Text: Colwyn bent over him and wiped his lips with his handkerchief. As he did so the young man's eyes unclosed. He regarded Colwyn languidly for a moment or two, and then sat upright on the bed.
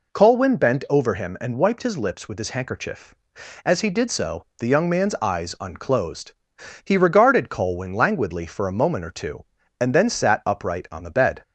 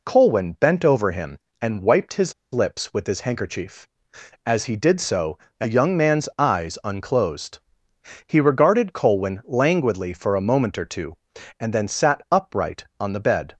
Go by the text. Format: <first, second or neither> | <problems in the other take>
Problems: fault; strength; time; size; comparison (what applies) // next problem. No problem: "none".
first | pauses between "his" and "lips"; slight; at 2.3 s; 0.19 s long // pauses between "so" and "the"; slight; at 5.3 s; 0.20 s long; slight in the first